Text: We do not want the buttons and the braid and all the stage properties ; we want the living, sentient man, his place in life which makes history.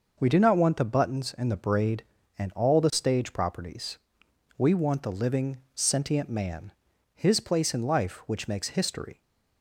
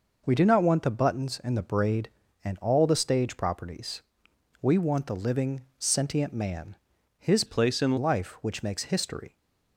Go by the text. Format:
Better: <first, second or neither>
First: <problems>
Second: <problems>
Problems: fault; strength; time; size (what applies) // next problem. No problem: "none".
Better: first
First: none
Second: changes voice from "place" to "in"; from 7.4 to 7.9 s; 0.5 s long